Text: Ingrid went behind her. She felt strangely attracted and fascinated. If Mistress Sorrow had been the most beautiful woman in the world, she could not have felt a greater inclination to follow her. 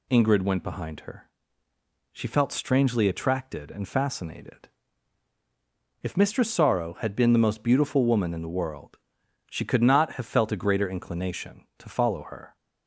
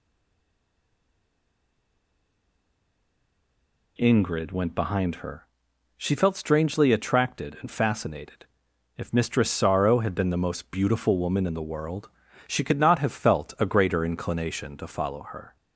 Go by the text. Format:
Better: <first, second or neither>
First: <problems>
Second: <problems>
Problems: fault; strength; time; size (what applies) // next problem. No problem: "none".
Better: first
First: none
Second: stays silent before the first word; strong; until 3.9 s; 3.9 s long